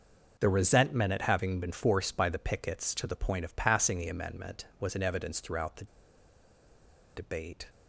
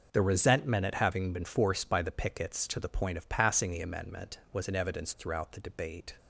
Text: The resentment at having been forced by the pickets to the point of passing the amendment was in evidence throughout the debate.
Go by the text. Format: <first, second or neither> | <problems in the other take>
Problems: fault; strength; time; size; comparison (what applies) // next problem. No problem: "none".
second | pauses between "the" and "debate"; strong; at 5.8 s; 1.3 s long